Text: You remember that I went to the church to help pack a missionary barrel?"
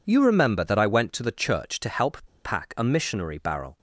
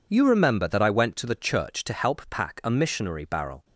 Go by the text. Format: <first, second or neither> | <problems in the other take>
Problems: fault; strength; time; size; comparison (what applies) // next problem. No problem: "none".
second | pauses between "help" and "pack"; slight; at 2.2 s; 0.20 s long